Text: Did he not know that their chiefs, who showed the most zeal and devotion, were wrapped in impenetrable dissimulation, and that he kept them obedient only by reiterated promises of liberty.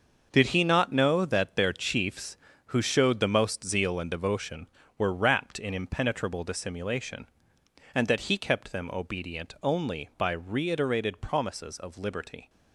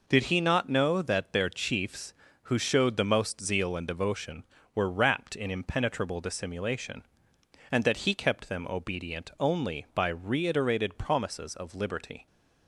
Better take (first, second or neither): second